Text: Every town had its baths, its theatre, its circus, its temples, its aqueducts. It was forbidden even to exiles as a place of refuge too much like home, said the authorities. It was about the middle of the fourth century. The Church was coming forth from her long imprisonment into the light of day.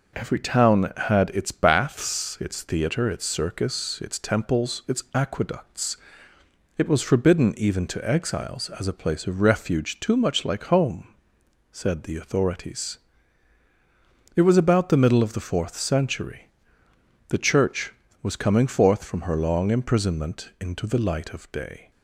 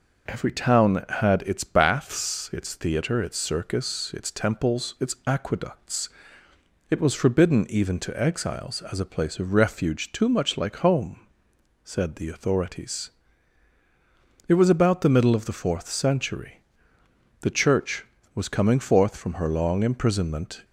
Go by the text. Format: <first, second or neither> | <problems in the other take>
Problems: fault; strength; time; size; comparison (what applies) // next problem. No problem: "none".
first | stops before "into the light of day"; at 20.6 s